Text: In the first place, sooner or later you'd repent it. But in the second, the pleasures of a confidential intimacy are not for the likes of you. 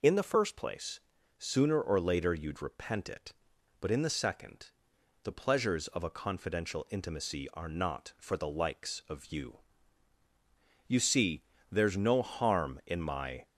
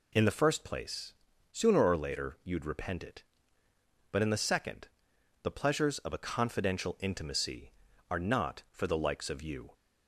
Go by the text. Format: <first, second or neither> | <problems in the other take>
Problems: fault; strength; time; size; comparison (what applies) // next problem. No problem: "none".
second | goes on to say "You see there's no harm in my"; strong; from 10.8 s on; 2.5 s long